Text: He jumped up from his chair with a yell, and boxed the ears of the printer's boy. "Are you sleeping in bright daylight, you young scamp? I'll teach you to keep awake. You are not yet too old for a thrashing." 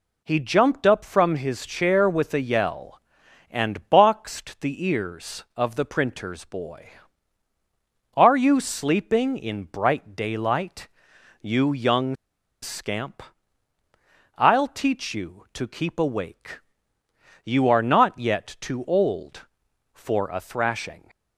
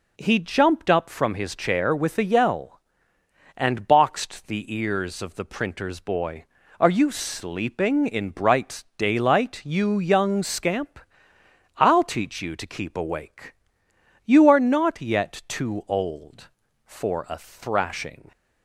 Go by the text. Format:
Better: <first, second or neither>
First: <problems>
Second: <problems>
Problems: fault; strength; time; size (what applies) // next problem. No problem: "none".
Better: second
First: pauses between "young" and "scamp"; noticeable; at 12.1 s; 0.47 s long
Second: none